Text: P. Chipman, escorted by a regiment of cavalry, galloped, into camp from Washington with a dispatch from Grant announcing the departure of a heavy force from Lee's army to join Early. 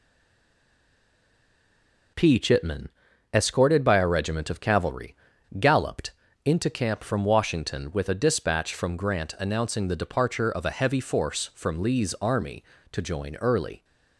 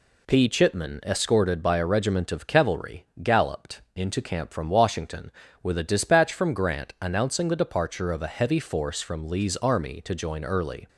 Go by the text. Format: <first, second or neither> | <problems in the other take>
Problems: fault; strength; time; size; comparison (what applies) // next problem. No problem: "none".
second | stays silent before the first word; until 2.1 s; 2.1 s long